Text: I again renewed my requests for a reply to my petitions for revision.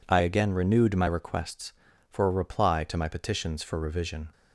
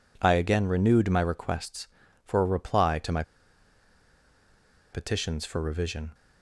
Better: first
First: none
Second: pauses between "my" and "petitions"; strong; at 3.2 s; 1.7 s long

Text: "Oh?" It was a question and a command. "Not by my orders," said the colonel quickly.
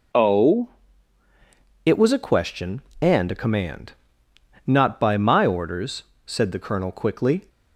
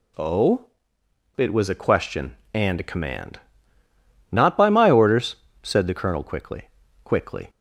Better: first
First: none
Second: says "quickly" twice; at 7.0 s

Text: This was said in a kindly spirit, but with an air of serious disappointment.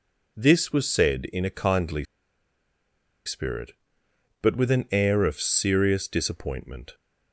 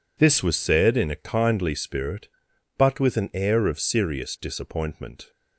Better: second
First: pauses between "kindly" and "spirit"; at 2.0 s; 1.2 s long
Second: none

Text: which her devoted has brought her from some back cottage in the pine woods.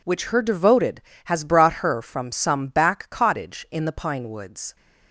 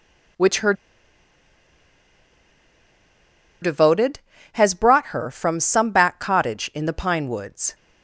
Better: first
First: none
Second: pauses between "her" and "devoted"; strong; at 0.7 s; 2.8 s long

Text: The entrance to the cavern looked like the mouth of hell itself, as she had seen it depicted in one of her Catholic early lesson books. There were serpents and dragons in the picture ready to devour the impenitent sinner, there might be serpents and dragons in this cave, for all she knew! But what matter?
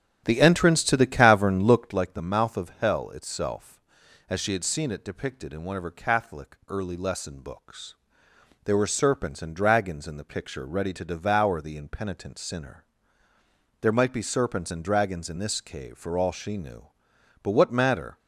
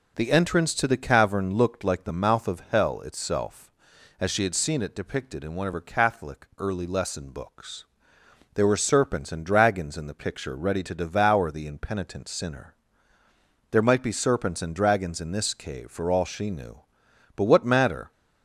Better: second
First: starts louder than the rest; strong; until 2.0 s; 10 dB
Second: none

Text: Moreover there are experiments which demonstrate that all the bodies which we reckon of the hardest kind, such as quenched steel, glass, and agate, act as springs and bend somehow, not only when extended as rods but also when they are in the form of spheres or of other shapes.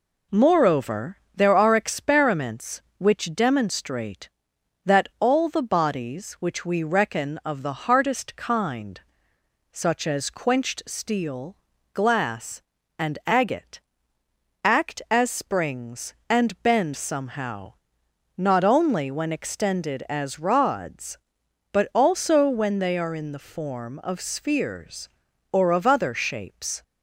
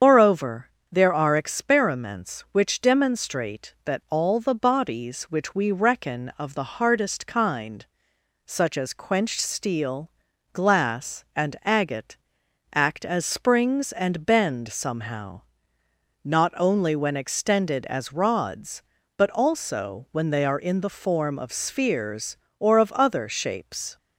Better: first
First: pauses between "Moreover" and "there"; slight; at 1.1 s; 0.18 s long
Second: loses the start of "Moreover"; at 0.0 s; 140 ms // starts louder than the rest; strong; until 1.2 s; 7.5 dB // pauses between "Moreover" and "there"; slight; at 0.6 s; 0.20 s long

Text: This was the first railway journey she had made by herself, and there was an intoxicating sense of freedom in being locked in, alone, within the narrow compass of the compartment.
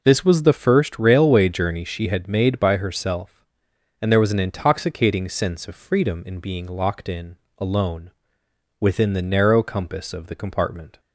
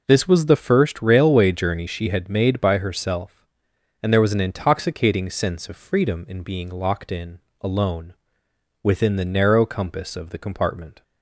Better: neither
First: none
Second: none

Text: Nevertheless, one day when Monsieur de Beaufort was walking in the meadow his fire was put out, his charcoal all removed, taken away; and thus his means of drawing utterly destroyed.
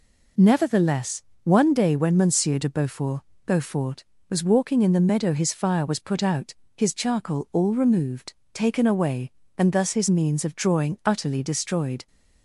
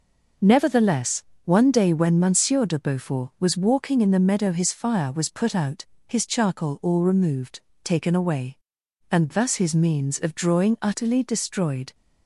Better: second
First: says "Beaufort" twice; at 3.4 s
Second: none

